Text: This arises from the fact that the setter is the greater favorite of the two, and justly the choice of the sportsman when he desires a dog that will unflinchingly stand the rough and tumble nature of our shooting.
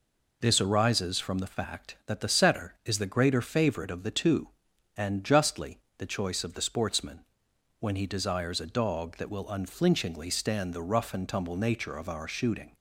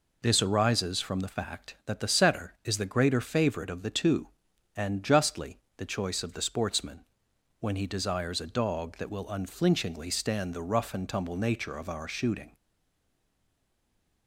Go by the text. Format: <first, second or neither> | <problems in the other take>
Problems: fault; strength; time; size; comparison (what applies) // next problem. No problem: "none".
first | pauses between "justly" and "the"; slight; at 5.5 s; 0.18 s long; slight in the first // pauses between "sportsman" and "when"; noticeable; at 7.0 s; 0.58 s long; noticeable in the first // stays silent after the last word; noticeable; from 12.5 s on; 1.7 s long